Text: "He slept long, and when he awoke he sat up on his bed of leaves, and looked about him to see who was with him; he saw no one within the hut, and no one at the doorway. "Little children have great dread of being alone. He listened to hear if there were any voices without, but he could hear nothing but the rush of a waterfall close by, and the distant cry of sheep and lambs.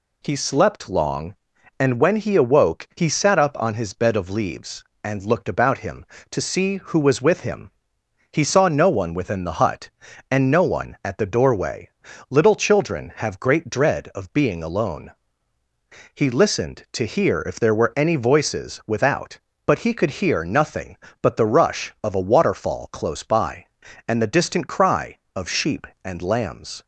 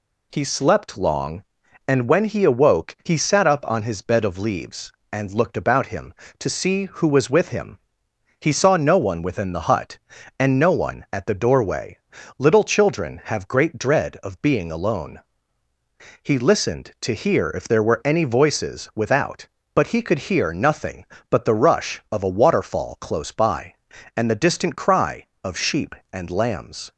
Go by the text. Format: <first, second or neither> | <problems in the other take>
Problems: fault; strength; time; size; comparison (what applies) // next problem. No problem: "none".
neither | none